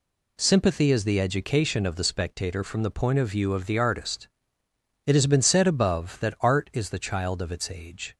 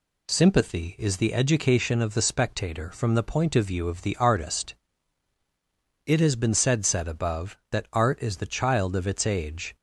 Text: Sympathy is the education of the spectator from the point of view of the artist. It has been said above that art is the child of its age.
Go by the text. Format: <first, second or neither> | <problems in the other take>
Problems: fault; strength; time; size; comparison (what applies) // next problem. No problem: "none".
first | says "said" twice; at 6.8 s